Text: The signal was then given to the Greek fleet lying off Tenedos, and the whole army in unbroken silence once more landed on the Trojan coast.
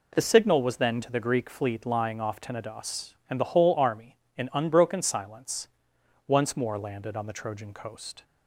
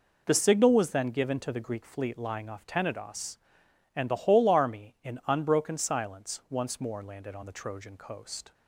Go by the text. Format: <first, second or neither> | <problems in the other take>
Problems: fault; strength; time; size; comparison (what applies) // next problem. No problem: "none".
second | skips "given"; at 1.0 s // pauses between "silence" and "once"; noticeable; at 5.6 s; 0.60 s long